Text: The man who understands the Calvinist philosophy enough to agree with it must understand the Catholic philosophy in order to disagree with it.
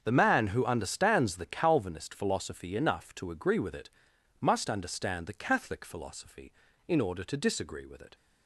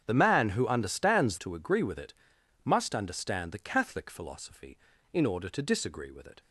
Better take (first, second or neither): first